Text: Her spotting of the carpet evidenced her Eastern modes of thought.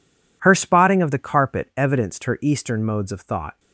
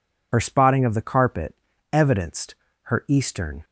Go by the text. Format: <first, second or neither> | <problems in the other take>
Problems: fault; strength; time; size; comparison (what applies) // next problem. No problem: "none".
first | pauses between "carpet" and "evidenced"; at 1.5 s; 0.38 s long // pauses between "evidenced" and "her"; slight; at 2.5 s; 0.30 s long // stops before "modes of thought"; at 3.6 s